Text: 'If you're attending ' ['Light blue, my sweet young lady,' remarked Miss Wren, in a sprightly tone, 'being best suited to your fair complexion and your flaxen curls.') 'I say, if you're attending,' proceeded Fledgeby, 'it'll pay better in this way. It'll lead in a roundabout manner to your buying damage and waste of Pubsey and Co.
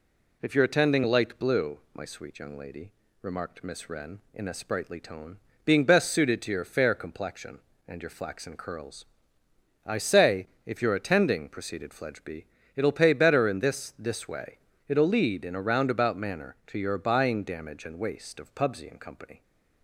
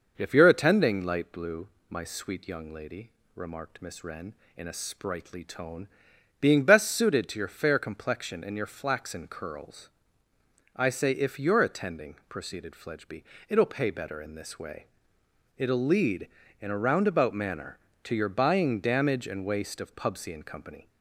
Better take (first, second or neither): second